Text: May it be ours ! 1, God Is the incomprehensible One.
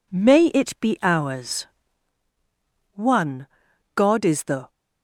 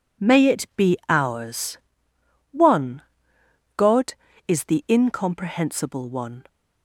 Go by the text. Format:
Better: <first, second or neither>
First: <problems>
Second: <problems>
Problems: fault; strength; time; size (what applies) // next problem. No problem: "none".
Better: second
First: stops before "incomprehensible One"; at 4.6 s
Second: none